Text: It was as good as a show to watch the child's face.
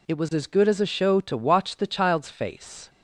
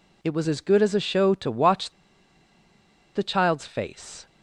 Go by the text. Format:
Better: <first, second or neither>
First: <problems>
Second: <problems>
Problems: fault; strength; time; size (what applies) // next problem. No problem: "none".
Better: first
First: none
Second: pauses between "watch" and "the"; at 1.9 s; 1.2 s long